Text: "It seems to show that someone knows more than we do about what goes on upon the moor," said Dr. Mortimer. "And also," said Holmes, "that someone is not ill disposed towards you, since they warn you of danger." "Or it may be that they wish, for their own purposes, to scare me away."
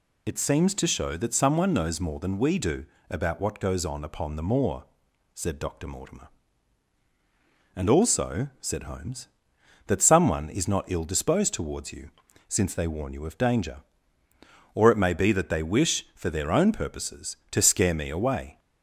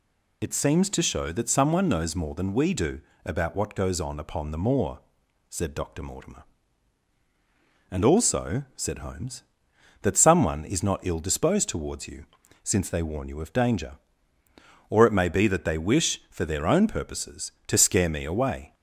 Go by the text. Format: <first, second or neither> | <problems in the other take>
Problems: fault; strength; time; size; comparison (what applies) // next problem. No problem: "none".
neither | pauses between "do" and "about"; slight; the same in both